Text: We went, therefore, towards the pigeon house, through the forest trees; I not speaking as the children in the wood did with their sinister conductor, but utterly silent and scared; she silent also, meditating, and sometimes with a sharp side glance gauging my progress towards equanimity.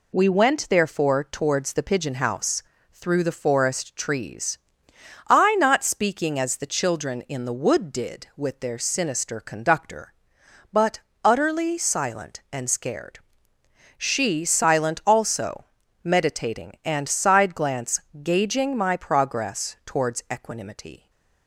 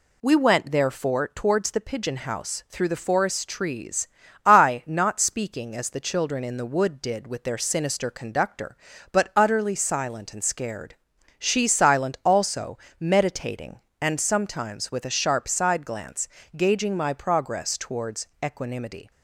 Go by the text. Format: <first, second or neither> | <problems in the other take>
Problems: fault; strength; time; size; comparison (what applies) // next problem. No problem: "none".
second | pauses between "but" and "utterly"; slight; at 10.9 s; 0.24 s long // skips "sometimes with a sharp"; at 17.0 s // pauses between "glance" and "gauging"; slight; at 17.9 s; 0.22 s long; slight in the second // stays silent after the last word; slight; from 20.9 s on; 0.5 s long